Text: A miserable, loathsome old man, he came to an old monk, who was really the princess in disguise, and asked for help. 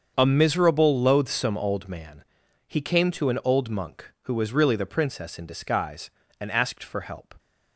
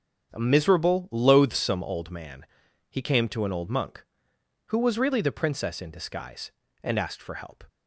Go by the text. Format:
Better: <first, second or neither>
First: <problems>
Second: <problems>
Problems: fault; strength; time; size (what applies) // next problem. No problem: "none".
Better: neither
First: starts louder than the rest; until 1.1 s; 7 dB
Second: starts louder than the rest; strong; until 1.3 s; 7.5 dB